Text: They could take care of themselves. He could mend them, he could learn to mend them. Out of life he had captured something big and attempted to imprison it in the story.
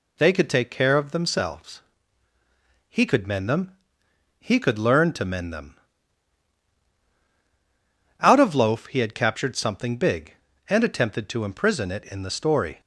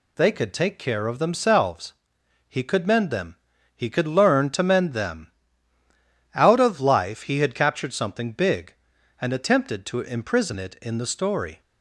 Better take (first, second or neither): second